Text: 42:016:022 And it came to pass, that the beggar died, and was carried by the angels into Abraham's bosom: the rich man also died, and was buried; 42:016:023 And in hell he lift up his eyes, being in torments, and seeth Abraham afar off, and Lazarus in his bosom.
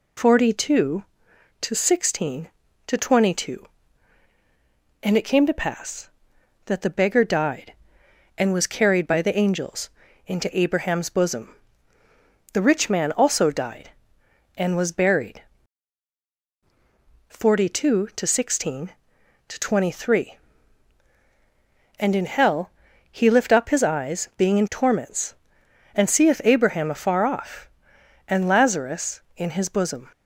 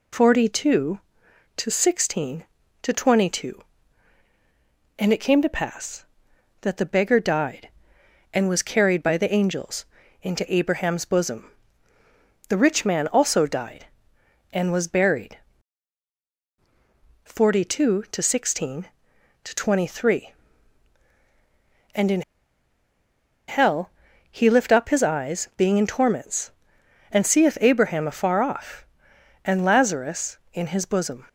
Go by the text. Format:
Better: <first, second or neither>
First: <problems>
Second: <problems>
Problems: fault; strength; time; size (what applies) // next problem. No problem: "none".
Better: first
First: pauses between "angels" and "into"; slight; at 9.8 s; 0.36 s long // pauses between "hell" and "he"; slight; at 22.7 s; 0.36 s long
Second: pauses between "angels" and "into"; slight; at 9.8 s; 0.36 s long // pauses between "in" and "hell"; strong; at 22.2 s; 1.2 s long // pauses between "hell" and "he"; slight; at 23.9 s; 0.36 s long